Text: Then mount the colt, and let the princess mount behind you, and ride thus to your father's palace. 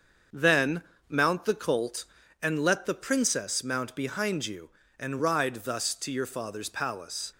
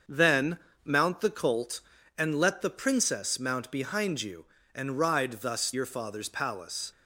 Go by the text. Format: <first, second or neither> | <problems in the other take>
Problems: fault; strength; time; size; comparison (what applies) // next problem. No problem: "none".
first | starts louder than the rest; until 1.3 s; 6.5 dB; also in the first // pauses between "Then" and "mount"; slight; at 0.5 s; 0.26 s long; slight in the first // skips "to"; at 5.7 s